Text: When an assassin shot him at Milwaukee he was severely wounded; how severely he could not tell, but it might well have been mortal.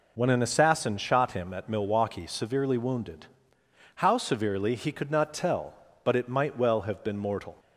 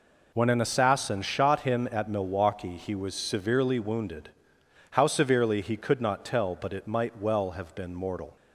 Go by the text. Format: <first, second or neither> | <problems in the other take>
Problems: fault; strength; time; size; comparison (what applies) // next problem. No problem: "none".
second | skips "he was"; at 2.2 s